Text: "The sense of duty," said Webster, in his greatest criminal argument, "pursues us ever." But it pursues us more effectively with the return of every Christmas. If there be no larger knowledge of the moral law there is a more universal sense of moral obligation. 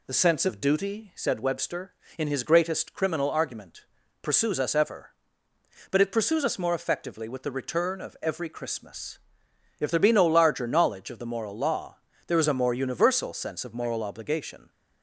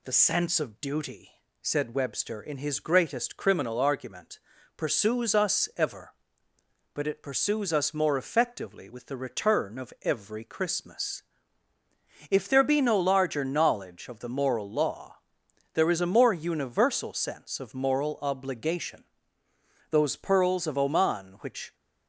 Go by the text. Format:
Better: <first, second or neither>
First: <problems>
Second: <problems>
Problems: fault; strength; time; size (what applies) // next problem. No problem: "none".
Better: first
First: pauses between "law" and "there"; slight; at 11.9 s; 0.28 s long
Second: pauses between "law" and "there"; noticeable; at 15.1 s; 0.56 s long // goes on to say "Those pearls of Oman which"; strong; from 19.9 s on; 1.8 s long